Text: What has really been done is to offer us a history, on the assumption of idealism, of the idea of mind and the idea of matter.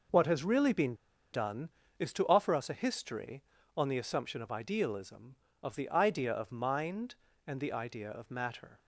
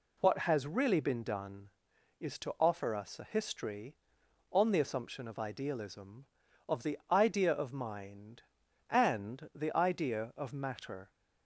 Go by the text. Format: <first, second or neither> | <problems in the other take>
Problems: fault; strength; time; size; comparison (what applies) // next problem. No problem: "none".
second | pauses between "been" and "done"; at 0.9 s; 0.38 s long